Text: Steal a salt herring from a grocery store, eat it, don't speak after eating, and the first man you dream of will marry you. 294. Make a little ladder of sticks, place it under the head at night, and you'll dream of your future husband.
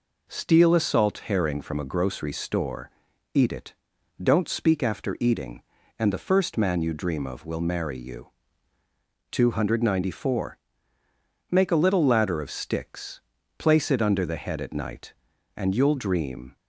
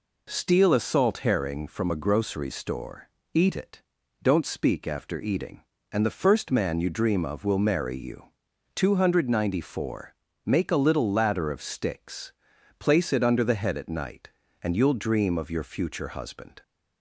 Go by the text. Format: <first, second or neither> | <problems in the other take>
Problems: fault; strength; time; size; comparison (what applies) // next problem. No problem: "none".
second | stops before "of your future husband"; at 16.5 s